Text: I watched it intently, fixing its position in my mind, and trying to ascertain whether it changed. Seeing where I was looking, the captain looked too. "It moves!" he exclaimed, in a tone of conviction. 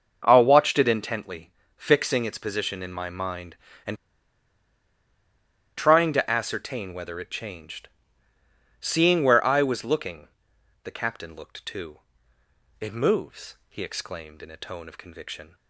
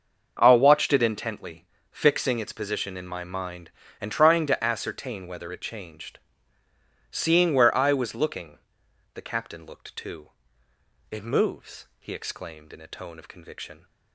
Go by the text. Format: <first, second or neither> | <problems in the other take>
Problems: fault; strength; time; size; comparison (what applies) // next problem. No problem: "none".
second | starts louder than the rest; until 1.2 s; 6.5 dB; also in the second // pauses between "and" and "trying"; strong; at 3.9 s; 1.8 s long